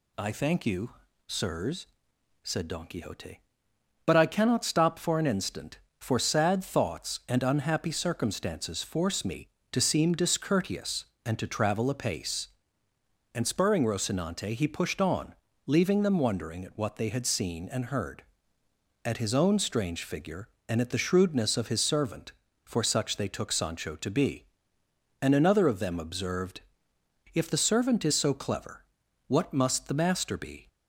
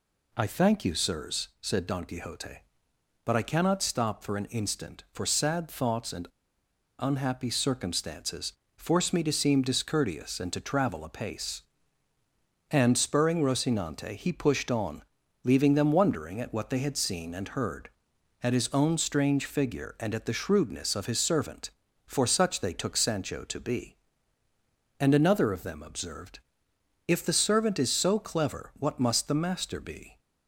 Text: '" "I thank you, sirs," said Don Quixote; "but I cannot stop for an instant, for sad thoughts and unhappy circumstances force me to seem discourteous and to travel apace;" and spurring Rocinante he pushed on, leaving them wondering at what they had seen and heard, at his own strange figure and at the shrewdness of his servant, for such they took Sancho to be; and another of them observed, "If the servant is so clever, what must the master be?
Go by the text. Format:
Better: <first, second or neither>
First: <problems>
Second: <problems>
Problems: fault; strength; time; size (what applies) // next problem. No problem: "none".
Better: first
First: none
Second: pauses between "and" and "unhappy"; noticeable; at 6.2 s; 0.72 s long // pauses between "circumstances" and "force"; slight; at 8.5 s; 0.24 s long